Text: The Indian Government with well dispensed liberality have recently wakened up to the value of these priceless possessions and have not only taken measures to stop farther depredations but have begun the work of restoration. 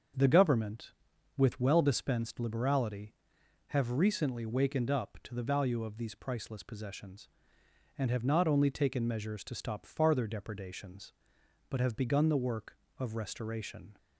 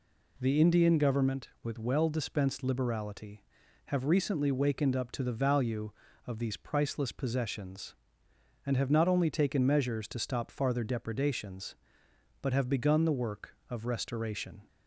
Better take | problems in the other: second | starts louder than the rest; until 1.6 s; 6.5 dB // skips "Indian"; at 0.2 s

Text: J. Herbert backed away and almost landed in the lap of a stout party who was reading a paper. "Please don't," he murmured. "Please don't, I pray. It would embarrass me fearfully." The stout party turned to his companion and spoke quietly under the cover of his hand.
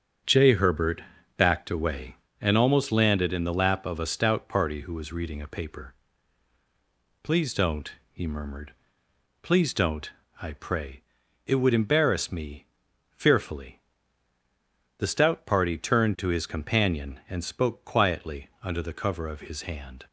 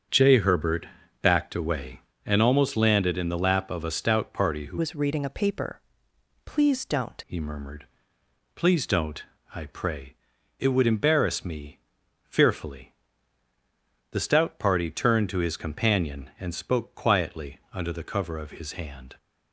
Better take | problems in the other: first | starts louder than the rest; strong; until 1.4 s; 7.5 dB; strong in the first // pauses between "Herbert" and "backed"; slight; at 0.8 s; 0.34 s long; slight in the first // changes voice from "was" to "don't"; from 4.7 to 7.2 s; 2.5 s long // pauses between "me" and "fearfully"; at 11.7 s; 0.44 s long; also in the first

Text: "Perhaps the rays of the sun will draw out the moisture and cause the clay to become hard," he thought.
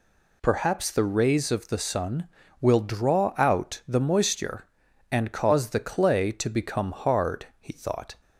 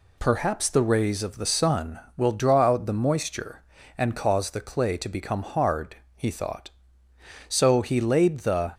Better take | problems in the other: first | goes on to say "So he laid the"; noticeable; from 7.4 s on; 1.2 s long

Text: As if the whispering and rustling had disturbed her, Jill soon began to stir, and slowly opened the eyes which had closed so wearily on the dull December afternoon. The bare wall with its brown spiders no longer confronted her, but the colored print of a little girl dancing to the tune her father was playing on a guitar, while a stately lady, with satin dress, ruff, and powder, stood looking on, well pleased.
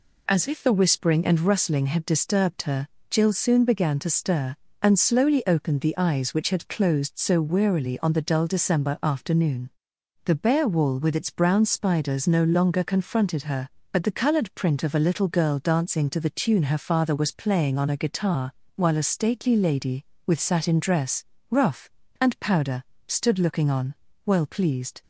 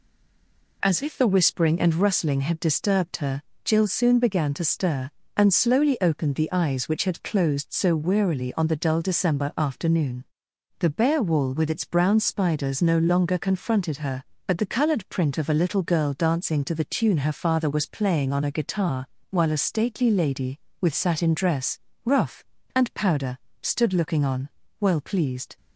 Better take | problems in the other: first | stays silent before the first word; slight; until 0.8 s; 0.8 s long

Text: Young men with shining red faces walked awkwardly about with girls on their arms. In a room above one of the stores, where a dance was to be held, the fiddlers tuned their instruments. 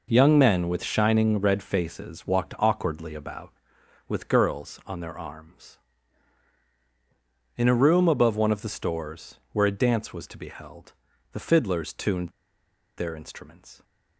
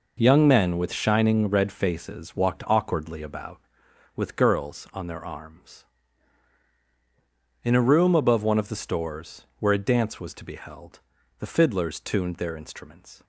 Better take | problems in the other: second | pauses between "tuned" and "their"; noticeable; at 12.2 s; 0.68 s long

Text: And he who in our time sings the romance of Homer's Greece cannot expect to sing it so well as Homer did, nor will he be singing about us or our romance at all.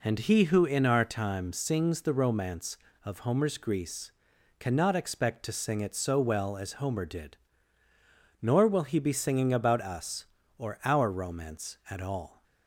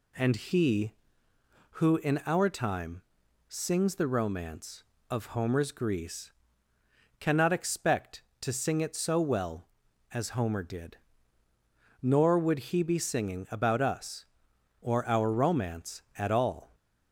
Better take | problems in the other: first | pauses between "time" and "sings"; noticeable; at 3.0 s; 0.46 s long // pauses between "Greece" and "cannot"; noticeable; at 6.3 s; 0.88 s long; noticeable in the first // says "would" for "will"; at 12.3 s

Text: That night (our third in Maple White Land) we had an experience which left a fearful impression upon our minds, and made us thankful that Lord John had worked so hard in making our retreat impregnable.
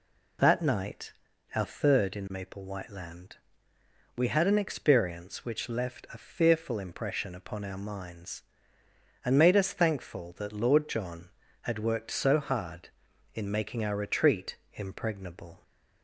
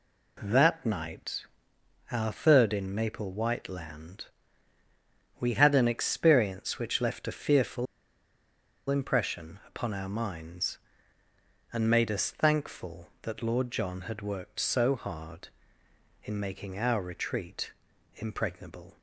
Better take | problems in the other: first | pauses between "fearful" and "impression"; at 7.8 s; 1.0 s long // pauses between "retreat" and "impregnable"; at 17.7 s; 0.44 s long; slight in the first

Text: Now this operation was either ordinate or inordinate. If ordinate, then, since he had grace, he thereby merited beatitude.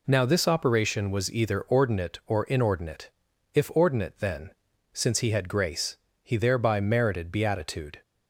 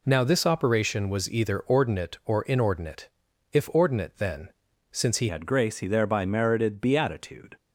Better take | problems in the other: first | changes voice at "had"; from 5.2 s on; 2.3 s long

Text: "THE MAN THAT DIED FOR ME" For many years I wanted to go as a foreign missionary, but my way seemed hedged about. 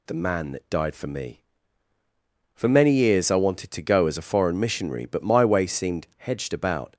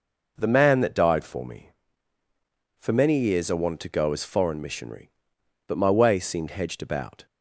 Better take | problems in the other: first | skips "a"; at 4.2 s

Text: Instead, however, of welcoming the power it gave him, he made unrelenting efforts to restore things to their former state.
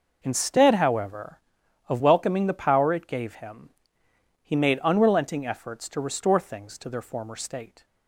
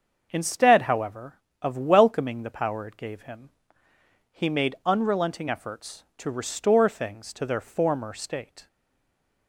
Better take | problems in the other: first | starts louder than the rest; until 1.3 s; 6.5 dB // stays silent after the last word; slight; from 8.6 s on; 0.8 s long

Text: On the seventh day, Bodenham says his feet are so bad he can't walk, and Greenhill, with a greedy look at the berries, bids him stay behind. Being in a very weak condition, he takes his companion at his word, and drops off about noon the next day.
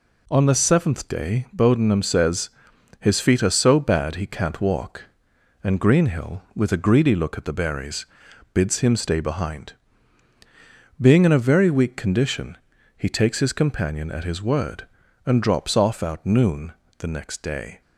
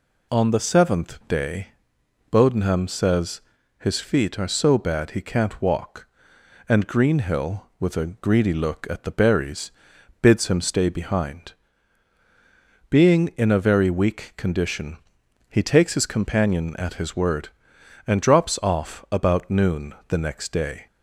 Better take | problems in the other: second | pauses between "says" and "his"; noticeable; at 2.4 s; 0.50 s long; also in the second // says "out" for "about"; at 16.0 s // pauses between "noon" and "the"; slight; at 16.7 s; 0.26 s long; slight in the second

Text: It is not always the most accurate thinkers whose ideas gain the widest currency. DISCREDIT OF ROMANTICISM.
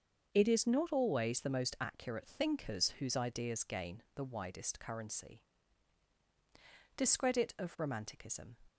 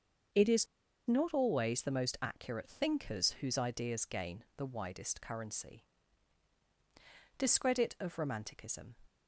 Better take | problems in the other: first | starts louder than the rest; until 1.7 s; 7 dB; also in the first // pauses between "is" and "not"; at 0.6 s; 0.41 s long

